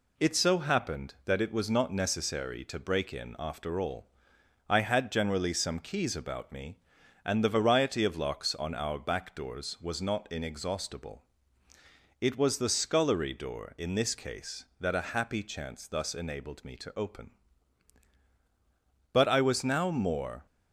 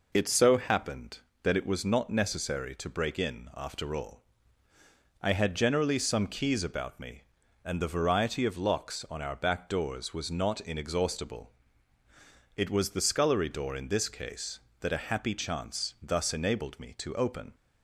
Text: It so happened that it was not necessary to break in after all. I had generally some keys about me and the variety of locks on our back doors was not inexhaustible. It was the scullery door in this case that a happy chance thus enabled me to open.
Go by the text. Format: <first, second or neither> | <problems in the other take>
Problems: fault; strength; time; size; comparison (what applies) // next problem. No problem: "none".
second | goes on to say "But I was now more"; from 19.1 s on; 1.3 s long